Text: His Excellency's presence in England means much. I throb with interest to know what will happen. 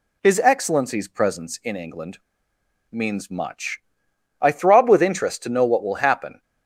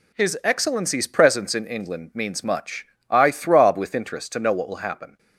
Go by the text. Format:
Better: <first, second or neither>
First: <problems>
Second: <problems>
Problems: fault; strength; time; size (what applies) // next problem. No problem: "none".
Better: second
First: pauses between "England" and "means"; noticeable; at 2.1 s; 0.73 s long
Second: none